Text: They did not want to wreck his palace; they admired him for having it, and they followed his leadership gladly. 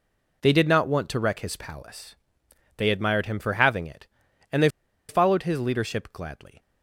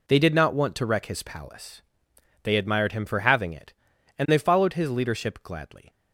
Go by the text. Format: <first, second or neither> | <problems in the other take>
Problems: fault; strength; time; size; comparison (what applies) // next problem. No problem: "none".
second | pauses between "they" and "followed"; at 4.6 s; 0.40 s long